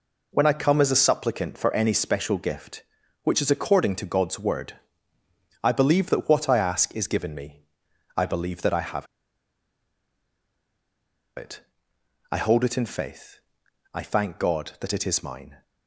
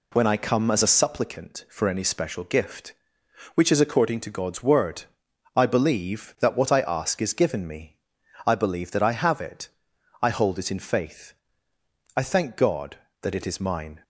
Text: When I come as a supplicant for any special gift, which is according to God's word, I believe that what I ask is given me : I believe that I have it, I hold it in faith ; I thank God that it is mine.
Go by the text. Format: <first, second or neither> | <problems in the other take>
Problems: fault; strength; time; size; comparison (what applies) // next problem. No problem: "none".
second | pauses between "have" and "it"; strong; at 9.0 s; 2.3 s long